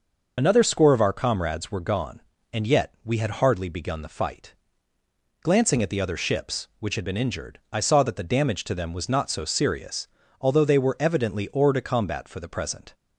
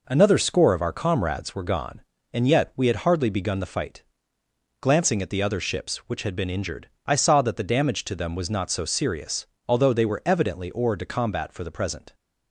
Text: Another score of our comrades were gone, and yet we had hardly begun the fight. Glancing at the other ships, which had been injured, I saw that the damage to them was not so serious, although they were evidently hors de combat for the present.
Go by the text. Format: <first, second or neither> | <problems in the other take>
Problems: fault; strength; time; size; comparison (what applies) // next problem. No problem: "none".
second | loses the start of "Another"; at 0.3 s; 40 ms